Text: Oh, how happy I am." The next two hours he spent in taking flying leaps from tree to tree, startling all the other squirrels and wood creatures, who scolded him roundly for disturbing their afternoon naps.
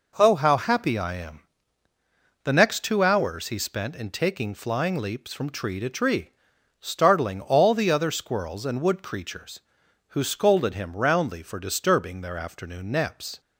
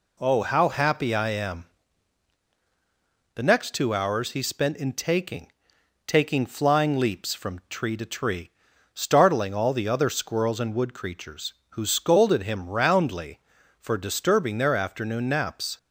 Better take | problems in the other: first | says "taking" twice; at 6.0 s

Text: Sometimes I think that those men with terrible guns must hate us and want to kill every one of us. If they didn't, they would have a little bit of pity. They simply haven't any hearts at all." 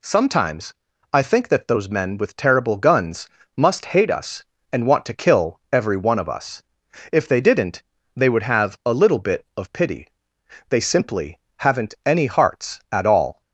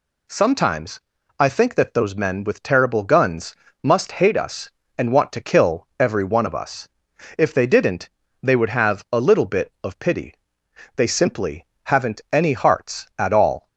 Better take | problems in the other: neither | pauses between "Sometimes" and "I"; slight; the same in both // pauses between "guns" and "must"; slight; the same in both // pauses between "simply" and "haven't"; slight; the same in both

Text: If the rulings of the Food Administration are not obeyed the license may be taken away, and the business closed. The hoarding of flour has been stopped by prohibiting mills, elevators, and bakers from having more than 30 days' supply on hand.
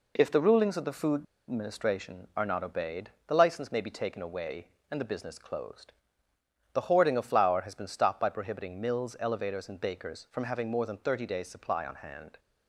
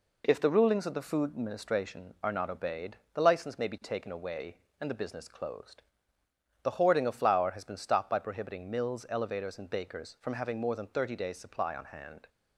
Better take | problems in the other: second | pauses between "Food" and "Administration"; slight; at 1.2 s; 0.28 s long // pauses between "obeyed" and "the"; slight; at 3.0 s; 0.18 s long; slight in the second

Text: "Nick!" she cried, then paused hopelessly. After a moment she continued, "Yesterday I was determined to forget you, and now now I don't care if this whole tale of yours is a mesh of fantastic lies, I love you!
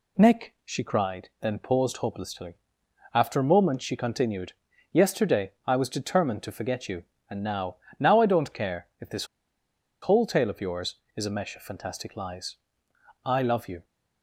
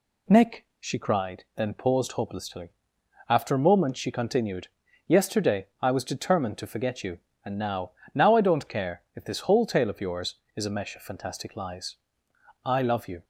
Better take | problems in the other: second | pauses between "Yesterday" and "I"; slight; at 5.5 s; 0.16 s long; slight in the second // pauses between "now" and "now"; slight; at 7.7 s; 0.24 s long; slight in the second // pauses between "this" and "whole"; noticeable; at 9.2 s; 0.77 s long

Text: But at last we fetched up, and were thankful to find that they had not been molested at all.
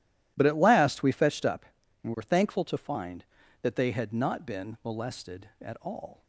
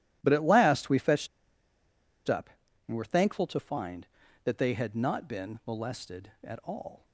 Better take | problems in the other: first | pauses between "fetched" and "up"; at 1.2 s; 1.0 s long

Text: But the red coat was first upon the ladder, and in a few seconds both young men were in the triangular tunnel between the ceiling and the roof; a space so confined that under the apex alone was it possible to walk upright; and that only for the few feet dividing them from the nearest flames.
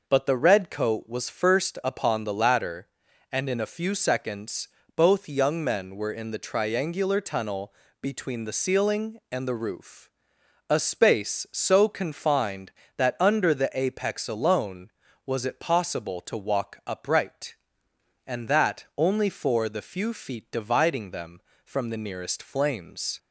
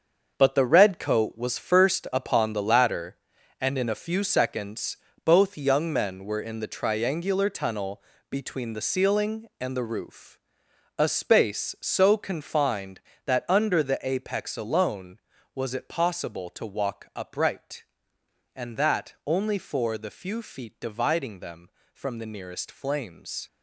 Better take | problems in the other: first | gets quieter; strong; throughout; 9.5 dB // pauses between "seconds" and "both"; slight; at 4.9 s; 0.26 s long; slight in the first // pauses between "tunnel" and "between"; slight; at 8.0 s; 0.28 s long; slight in the first

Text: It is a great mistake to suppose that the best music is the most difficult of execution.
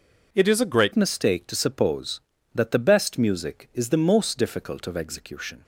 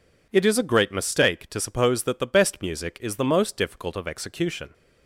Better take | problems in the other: second | changes voice at "mistake"; from 0.9 s on; 4.7 s long

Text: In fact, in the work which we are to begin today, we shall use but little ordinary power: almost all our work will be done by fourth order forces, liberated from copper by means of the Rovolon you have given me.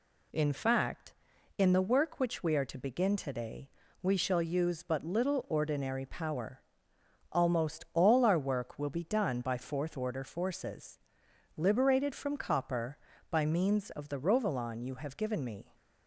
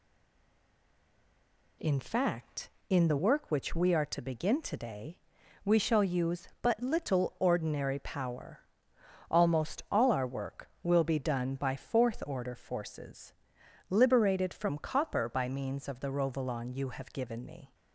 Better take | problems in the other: first | stays silent before the first word; noticeable; until 1.8 s; 1.8 s long

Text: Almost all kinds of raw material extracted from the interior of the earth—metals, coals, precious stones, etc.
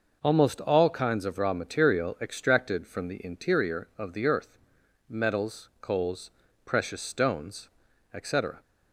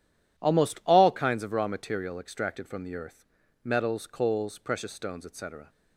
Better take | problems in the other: first | skips "the interior of"; at 2.8 s

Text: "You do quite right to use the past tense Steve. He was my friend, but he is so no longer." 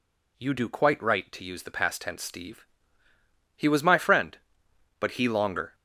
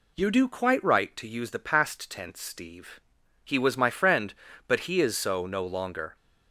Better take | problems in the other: second | skips "is so no"; at 5.2 s

